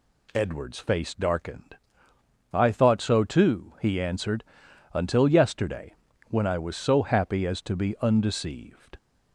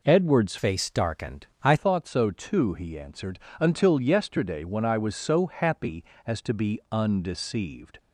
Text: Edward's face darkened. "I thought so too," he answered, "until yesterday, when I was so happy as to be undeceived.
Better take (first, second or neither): first